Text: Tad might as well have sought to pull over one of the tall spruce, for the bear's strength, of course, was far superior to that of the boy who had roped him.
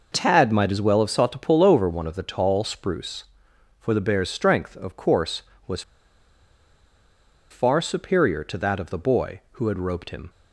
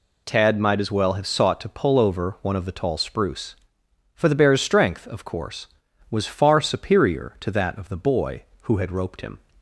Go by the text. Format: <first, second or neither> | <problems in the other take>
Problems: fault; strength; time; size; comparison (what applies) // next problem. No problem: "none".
second | pauses between "was" and "far"; strong; at 5.8 s; 1.6 s long